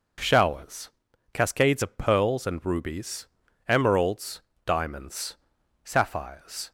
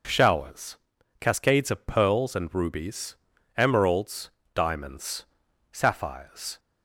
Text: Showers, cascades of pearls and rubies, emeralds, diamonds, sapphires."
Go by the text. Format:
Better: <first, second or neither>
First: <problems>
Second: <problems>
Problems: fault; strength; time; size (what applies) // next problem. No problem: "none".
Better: neither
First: none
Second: none